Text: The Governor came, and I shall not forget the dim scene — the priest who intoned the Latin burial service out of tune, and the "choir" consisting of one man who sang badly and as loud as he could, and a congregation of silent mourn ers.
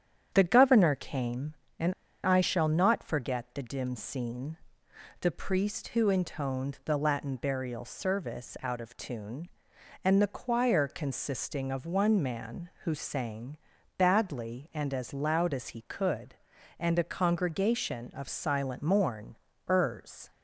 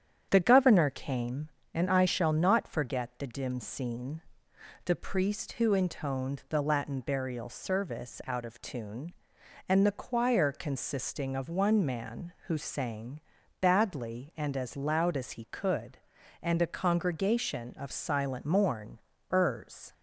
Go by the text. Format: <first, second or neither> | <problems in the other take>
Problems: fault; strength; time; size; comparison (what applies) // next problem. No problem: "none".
second | starts louder than the rest; strong; until 1.3 s; 8.5 dB; strong in the second // pauses between "and" and "I"; slight; at 1.9 s; 0.32 s long // pauses between "sang" and "badly"; at 13.5 s; 0.40 s long; also in the second // pauses between "mourn" and "ers"; slight; at 19.3 s; 0.32 s long; slight in the second